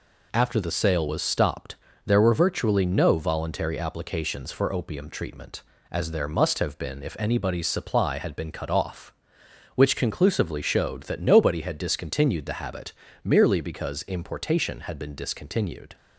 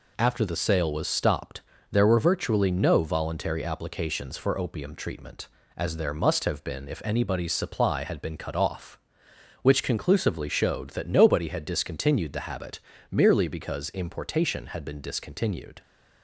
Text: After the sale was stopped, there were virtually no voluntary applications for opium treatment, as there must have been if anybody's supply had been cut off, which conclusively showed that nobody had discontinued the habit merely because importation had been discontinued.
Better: neither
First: pauses between "habit" and "merely"; slight; at 12.9 s; 0.32 s long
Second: pauses between "habit" and "merely"; slight; at 12.7 s; 0.32 s long

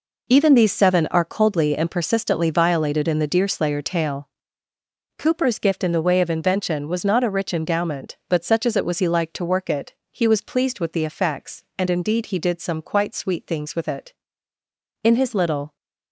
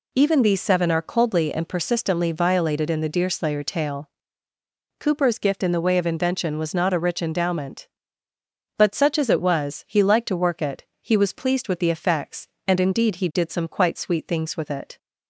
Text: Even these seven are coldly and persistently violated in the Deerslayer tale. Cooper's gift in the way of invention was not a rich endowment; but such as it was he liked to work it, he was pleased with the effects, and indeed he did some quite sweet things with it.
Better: second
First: goes on to say "In his little"; noticeable; from 15.0 s on; 0.72 s long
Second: none

